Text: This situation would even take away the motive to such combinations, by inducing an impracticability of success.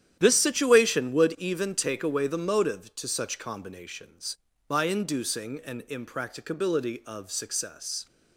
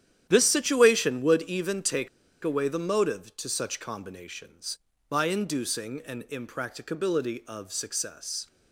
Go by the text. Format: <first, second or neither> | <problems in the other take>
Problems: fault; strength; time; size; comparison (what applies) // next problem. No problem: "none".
first | starts louder than the rest; strong; until 1.3 s; 10.5 dB; strong in the first // pauses between "take" and "away"; at 2.0 s; 0.36 s long